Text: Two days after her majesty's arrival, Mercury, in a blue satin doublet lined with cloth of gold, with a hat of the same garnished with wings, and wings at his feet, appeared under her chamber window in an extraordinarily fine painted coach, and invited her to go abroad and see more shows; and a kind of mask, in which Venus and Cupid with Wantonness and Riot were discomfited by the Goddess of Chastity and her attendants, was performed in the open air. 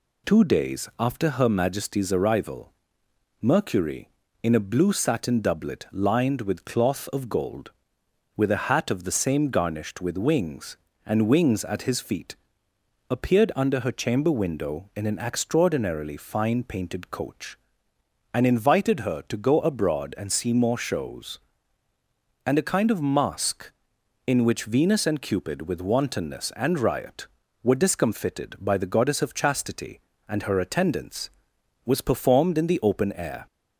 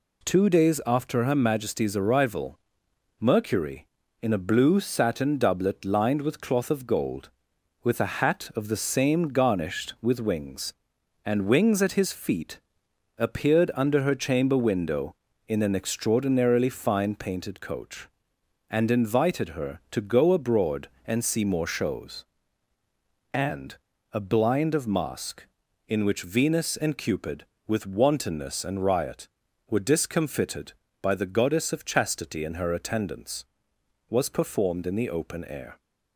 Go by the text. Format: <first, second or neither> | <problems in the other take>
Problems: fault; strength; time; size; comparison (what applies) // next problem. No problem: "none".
first | pauses between "and" and "a"; slight; at 23.7 s; 0.36 s long // says "blind" for "kind"; at 24.1 s